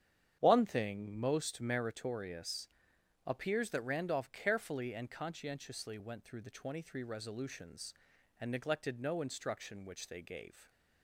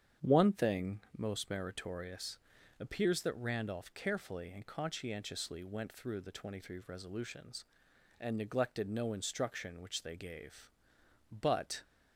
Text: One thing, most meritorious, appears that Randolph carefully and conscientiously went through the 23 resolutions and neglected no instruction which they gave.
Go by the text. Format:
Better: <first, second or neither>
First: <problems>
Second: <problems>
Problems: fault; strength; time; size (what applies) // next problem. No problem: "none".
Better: first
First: starts louder than the rest; strong; until 1.4 s; 9 dB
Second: starts louder than the rest; strong; until 1.3 s; 8.5 dB // goes on to say "But"; from 11.3 s on; 0.52 s long